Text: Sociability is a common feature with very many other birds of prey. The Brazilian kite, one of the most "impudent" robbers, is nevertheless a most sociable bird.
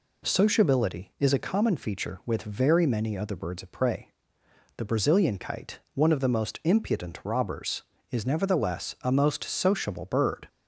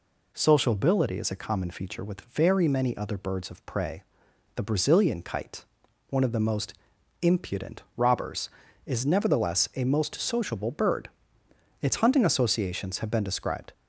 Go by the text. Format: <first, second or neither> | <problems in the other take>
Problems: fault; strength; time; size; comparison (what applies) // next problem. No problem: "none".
first | pauses between "most" and "impudent"; noticeable; at 6.7 s; 0.48 s long // pauses between "impudent" and "robbers"; slight; at 7.8 s; 0.16 s long // goes on to say "Its hunting associations have been described"; strong; from 11.8 s on; 1.9 s long